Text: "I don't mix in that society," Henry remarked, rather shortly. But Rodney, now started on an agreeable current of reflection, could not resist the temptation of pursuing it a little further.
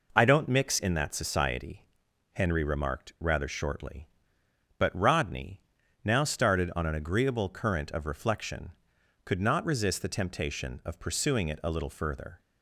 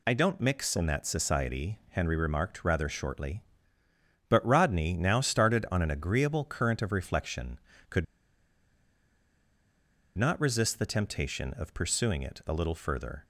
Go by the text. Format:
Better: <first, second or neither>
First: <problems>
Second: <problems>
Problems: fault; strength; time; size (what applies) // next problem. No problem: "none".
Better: first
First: none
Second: pauses between "could" and "not"; strong; at 8.0 s; 2.1 s long